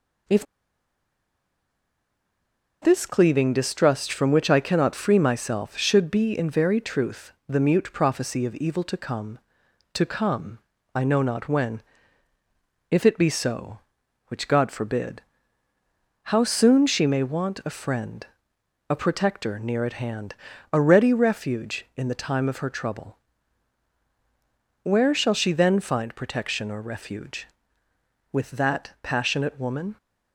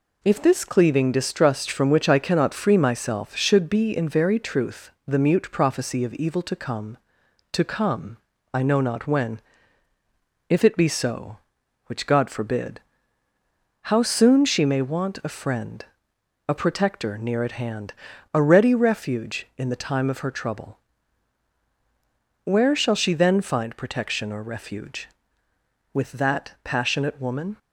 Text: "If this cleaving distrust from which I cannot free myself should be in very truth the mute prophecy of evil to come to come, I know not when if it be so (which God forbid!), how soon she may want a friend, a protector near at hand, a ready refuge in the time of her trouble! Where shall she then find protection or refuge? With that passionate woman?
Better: second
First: pauses between "If" and "this"; strong; at 0.4 s; 2.3 s long // pauses between "when" and "if"; at 11.8 s; 1.0 s long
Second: pauses between "when" and "if"; at 9.4 s; 1.0 s long

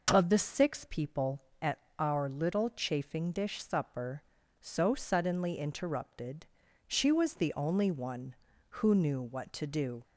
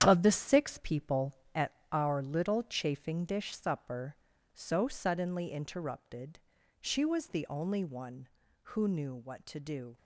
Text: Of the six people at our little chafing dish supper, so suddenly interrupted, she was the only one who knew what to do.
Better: first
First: pauses between "at" and "our"; slight; at 1.7 s; 0.22 s long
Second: gets quieter; strong; throughout; 9 dB // pauses between "at" and "our"; slight; at 1.7 s; 0.22 s long

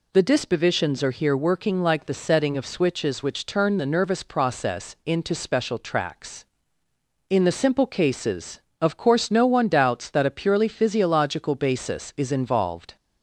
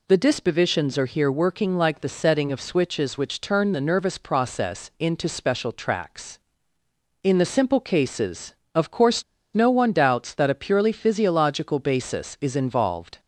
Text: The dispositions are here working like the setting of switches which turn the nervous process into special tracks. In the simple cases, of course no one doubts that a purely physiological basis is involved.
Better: first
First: none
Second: pauses between "course" and "no"; slight; at 9.2 s; 0.32 s long

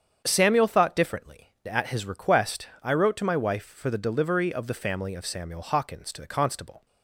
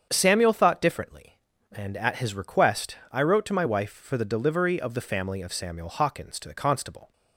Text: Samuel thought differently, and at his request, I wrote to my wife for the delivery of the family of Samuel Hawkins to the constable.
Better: second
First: starts louder than the rest; strong; until 1.2 s; 8 dB // skips "and"; at 1.5 s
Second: starts louder than the rest; strong; until 1.1 s; 7.5 dB

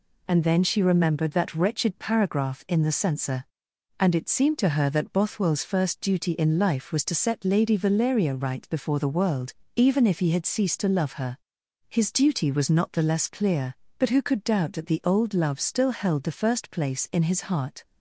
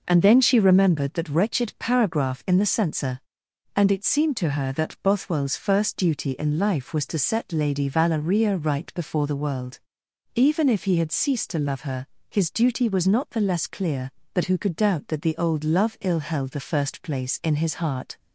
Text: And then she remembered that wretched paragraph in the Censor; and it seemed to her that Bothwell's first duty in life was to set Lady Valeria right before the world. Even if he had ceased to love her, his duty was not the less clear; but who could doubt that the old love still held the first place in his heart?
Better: first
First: none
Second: says "ill" for "still"; at 16.0 s

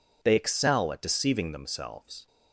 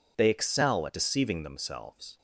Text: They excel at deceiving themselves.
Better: neither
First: none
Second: none

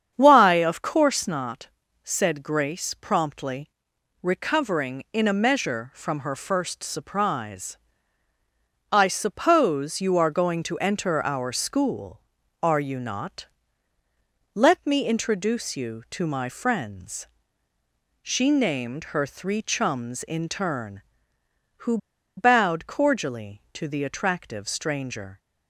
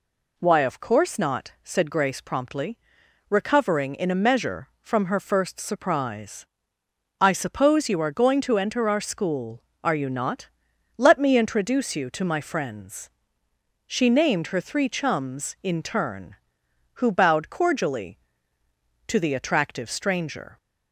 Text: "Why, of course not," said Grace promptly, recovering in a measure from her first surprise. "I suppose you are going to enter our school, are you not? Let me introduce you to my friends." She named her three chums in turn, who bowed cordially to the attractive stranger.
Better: second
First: starts louder than the rest; strong; until 1.1 s; 8 dB // pauses between "who" and "bowed"; at 21.9 s; 0.40 s long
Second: none

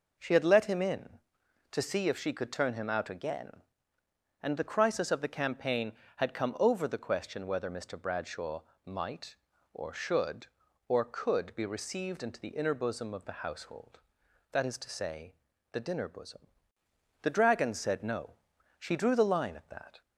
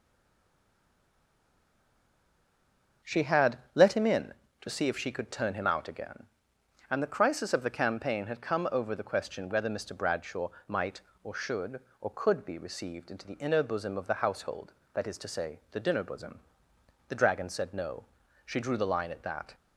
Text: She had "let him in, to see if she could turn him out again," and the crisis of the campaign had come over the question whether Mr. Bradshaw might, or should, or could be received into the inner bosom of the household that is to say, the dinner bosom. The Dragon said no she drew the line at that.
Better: first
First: pauses between "Bradshaw" and "might"; slight; at 8.6 s; 0.22 s long // pauses between "no" and "she"; at 18.3 s; 0.44 s long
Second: stays silent before the first word; strong; until 3.0 s; 3.0 s long // starts louder than the rest; until 4.2 s; 6.5 dB // pauses between "had" and "let"; slight; at 3.5 s; 0.16 s long // pauses between "Bradshaw" and "might"; slight; at 10.5 s; 0.18 s long // pauses between "no" and "she"; at 18.0 s; 0.40 s long

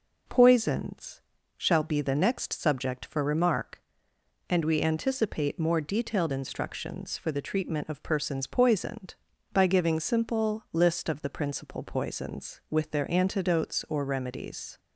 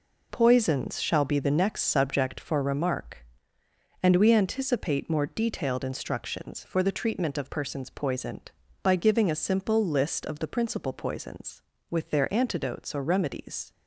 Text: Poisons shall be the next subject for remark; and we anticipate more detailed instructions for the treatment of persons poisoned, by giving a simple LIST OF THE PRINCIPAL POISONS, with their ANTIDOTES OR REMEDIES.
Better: second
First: pauses between "Poisons" and "shall"; slight; at 1.2 s; 0.36 s long // skips "a"; at 9.9 s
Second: none

